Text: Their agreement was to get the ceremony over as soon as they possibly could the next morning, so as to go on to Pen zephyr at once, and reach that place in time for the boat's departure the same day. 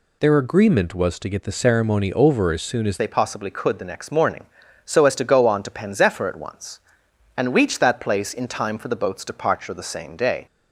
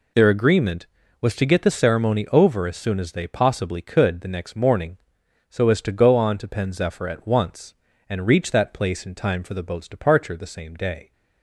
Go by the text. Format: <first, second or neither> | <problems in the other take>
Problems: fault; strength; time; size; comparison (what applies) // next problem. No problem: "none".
second | changes voice at "they"; from 2.9 s on; 7.5 s long